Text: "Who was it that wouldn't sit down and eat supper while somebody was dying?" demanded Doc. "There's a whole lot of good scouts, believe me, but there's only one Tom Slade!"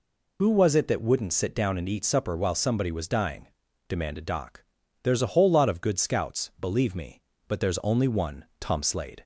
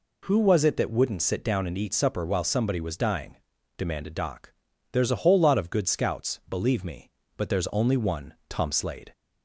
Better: second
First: loses the start of "Who"; at 0.3 s; 60 ms // pauses between "one" and "Tom"; slight; at 8.4 s; 0.16 s long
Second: pauses between "one" and "Tom"; slight; at 8.3 s; 0.16 s long

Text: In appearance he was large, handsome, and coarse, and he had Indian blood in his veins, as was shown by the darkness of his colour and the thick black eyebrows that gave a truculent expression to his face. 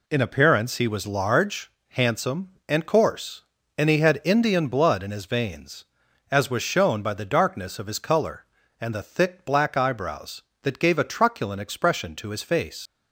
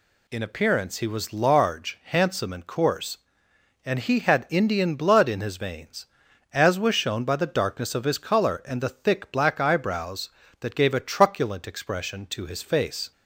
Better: second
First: leaves "face" unfinished; at 12.8 s; 80 ms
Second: none

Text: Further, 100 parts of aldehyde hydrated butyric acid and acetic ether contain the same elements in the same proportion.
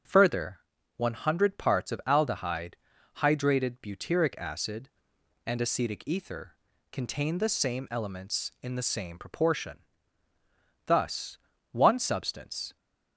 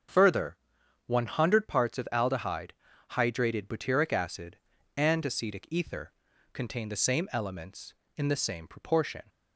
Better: second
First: starts louder than the rest; until 1.4 s; 6.5 dB // pauses between "aldehyde" and "hydrated"; at 2.7 s; 0.44 s long // pauses between "ether" and "contain"; at 6.5 s; 0.38 s long // goes on to say "Thus one substance"; strong; from 10.8 s on; 1.9 s long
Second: starts louder than the rest; strong; until 1.6 s; 7.5 dB // pauses between "aldehyde" and "hydrated"; at 2.7 s; 0.40 s long // pauses between "ether" and "contain"; at 6.1 s; 0.40 s long

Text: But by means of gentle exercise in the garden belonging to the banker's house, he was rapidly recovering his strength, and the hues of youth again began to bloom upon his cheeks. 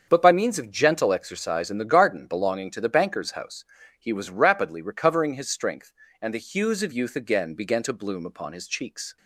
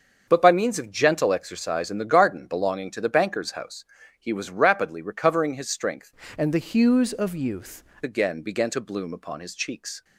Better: first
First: starts louder than the rest; until 1.1 s; 7 dB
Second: starts louder than the rest; until 1.2 s; 6.5 dB // changes voice from "and" to "youth"; from 6.3 to 7.8 s; 1.5 s long

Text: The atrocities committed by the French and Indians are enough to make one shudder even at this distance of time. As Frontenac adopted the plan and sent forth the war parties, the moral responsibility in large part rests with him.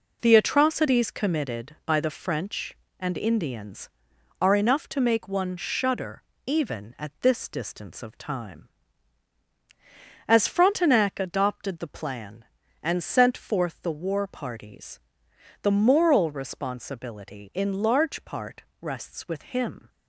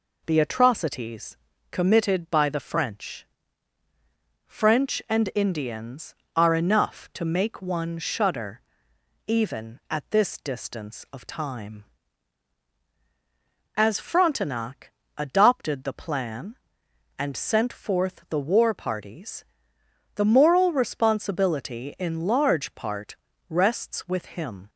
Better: first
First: pauses between "shudder" and "even"; slight; at 6.2 s; 0.24 s long // pauses between "part" and "rests"; slight; at 18.6 s; 0.22 s long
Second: pauses between "atrocities" and "committed"; slight; at 1.3 s; 0.36 s long // says "French" twice; at 4.4 s // pauses between "shudder" and "even"; noticeable; at 8.6 s; 0.66 s long // pauses between "Frontenac" and "adopted"; slight; at 14.9 s; 0.26 s long // pauses between "part" and "rests"; slight; at 23.1 s; 0.32 s long

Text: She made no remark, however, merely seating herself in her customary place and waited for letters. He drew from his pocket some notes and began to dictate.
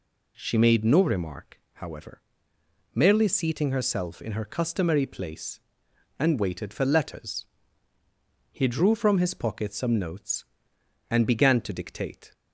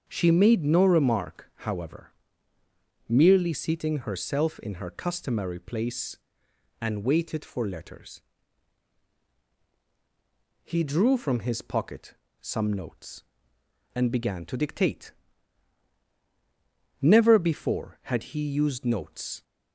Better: first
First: none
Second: starts louder than the rest; until 1.0 s; 7 dB // pauses between "pocket" and "some"; slight; at 12.1 s; 0.26 s long // goes on to say "Never before had he used notes"; strong; from 17.0 s on; 2.4 s long

